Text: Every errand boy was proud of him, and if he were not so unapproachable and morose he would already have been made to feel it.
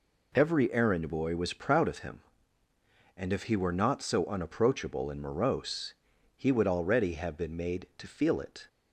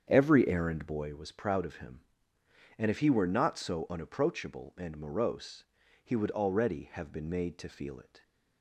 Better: first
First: pauses between "morose" and "he"; at 5.9 s; 0.42 s long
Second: starts louder than the rest; strong; until 1.3 s; 7.5 dB // pauses between "morose" and "he"; at 5.6 s; 0.38 s long

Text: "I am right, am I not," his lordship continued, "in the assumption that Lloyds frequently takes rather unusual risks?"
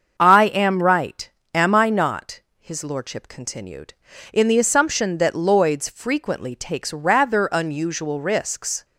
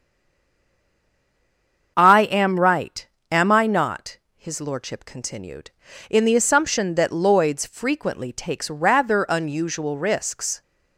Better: first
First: starts louder than the rest; until 1.1 s; 7 dB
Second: stays silent before the first word; noticeable; until 1.9 s; 1.9 s long // starts louder than the rest; until 2.9 s; 7 dB

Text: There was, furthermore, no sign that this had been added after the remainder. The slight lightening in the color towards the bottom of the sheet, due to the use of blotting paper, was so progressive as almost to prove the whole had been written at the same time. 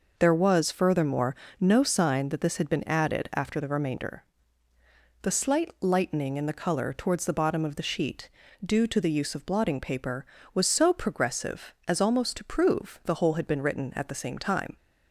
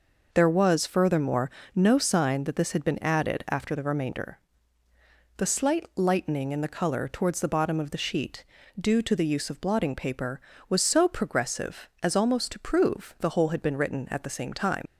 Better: first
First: none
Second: leaves "time" unfinished; at 14.8 s; 55 ms

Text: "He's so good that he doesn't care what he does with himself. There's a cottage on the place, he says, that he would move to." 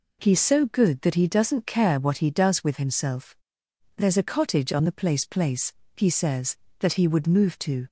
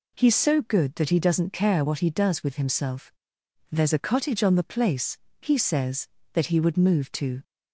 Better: second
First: says "place" twice; at 5.2 s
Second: none

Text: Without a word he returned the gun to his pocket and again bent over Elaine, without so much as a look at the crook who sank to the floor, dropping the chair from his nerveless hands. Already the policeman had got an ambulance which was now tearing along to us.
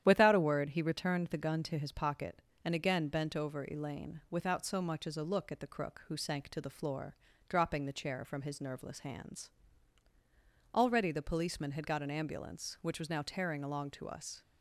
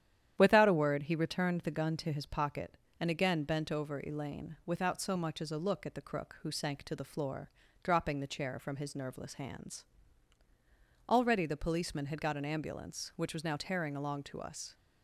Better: neither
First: starts louder than the rest; strong; until 1.0 s; 10.5 dB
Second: starts louder than the rest; strong; until 1.3 s; 10.5 dB

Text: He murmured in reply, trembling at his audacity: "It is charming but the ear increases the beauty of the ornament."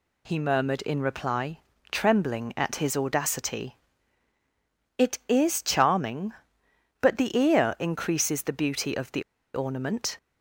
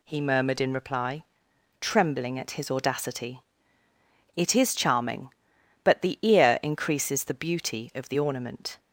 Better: second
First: pauses between "the" and "ornament"; slight; at 9.2 s; 0.32 s long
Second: none

